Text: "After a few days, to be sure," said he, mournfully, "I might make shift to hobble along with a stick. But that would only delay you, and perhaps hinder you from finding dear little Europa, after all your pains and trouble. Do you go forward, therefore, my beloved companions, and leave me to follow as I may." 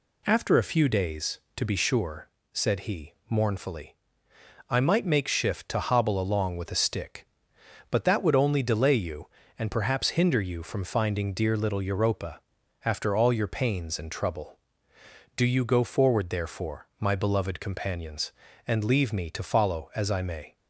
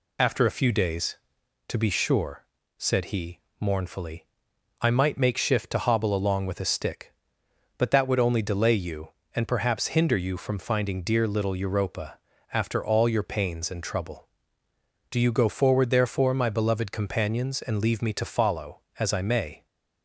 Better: first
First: none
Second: loses the start of "After"; at 0.1 s; 50 ms

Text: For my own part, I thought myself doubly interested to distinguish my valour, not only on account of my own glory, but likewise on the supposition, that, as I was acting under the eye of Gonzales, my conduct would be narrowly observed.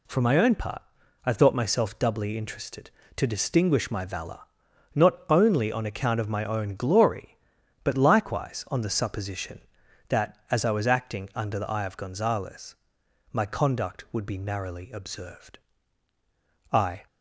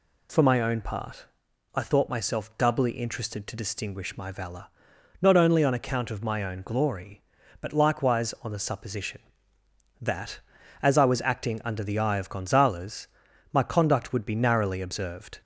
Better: second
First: goes on to say "I"; slight; from 16.7 s on; 0.34 s long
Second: none

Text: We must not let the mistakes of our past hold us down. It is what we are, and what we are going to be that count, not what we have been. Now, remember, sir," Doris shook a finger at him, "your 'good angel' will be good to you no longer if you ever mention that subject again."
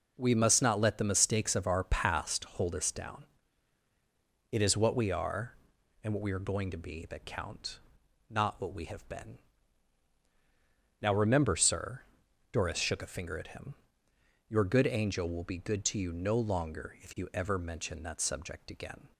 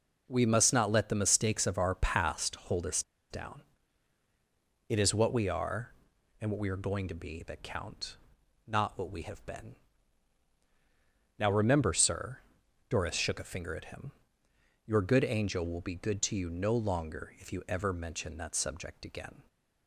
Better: first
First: none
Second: pauses between "us" and "down"; slight; at 3.0 s; 0.28 s long

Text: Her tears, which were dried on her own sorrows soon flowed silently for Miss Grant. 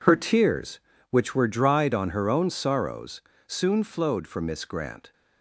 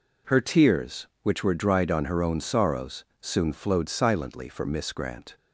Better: second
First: pauses between "sorrows" and "soon"; slight; at 3.2 s; 0.26 s long // skips "silently"; at 4.2 s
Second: pauses between "sorrows" and "soon"; slight; at 3.0 s; 0.16 s long

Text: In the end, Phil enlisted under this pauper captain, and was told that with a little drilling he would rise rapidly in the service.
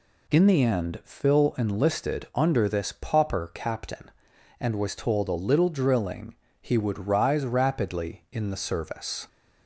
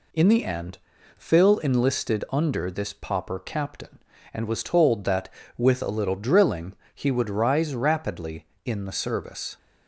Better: second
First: skips "that with"; at 5.2 s // pauses between "drilling" and "he"; slight; at 6.3 s; 0.26 s long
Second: pauses between "drilling" and "he"; slight; at 6.7 s; 0.20 s long

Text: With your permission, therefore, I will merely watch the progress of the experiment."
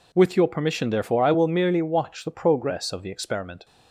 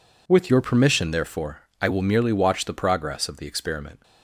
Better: first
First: none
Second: changes voice at "your"; from 0.4 s on; 3.5 s long

